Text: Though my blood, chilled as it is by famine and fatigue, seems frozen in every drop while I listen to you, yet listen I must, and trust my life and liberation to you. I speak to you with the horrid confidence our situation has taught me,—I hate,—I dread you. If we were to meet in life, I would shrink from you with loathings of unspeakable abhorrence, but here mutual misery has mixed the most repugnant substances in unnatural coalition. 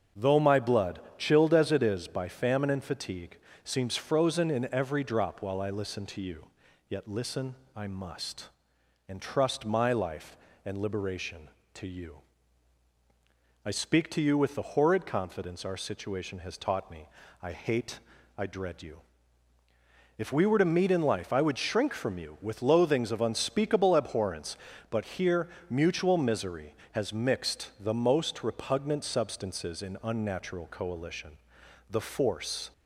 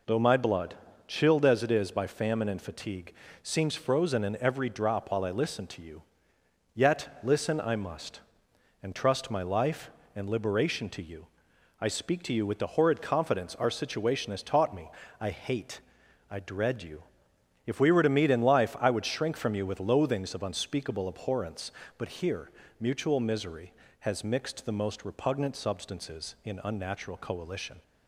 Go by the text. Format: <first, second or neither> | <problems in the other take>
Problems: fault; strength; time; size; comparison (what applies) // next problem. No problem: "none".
second | starts louder than the rest; until 1.3 s; 7 dB // pauses between "listen" and "I"; slight; at 7.5 s; 0.22 s long // pauses between "here" and "mutual"; slight; at 25.4 s; 0.22 s long; slight in the second // goes on to say "The force"; noticeable; from 31.8 s on; 0.80 s long